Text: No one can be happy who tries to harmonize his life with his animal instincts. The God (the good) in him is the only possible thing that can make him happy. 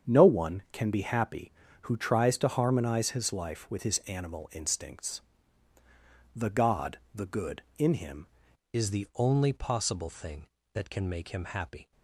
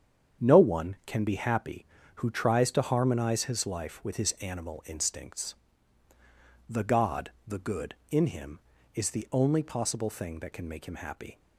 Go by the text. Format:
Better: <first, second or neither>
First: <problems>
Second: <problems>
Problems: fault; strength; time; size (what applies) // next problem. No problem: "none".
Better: second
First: starts louder than the rest; strong; until 1.1 s; 7.5 dB // changes voice at "is"; from 8.7 s on; 3.2 s long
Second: starts louder than the rest; strong; until 1.5 s; 8 dB